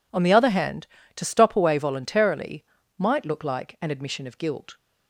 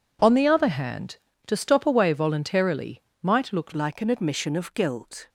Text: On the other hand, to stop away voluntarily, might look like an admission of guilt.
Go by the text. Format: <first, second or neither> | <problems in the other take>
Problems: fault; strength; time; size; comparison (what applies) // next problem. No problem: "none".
first | changes voice at "like"; from 3.7 s on; 1.5 s long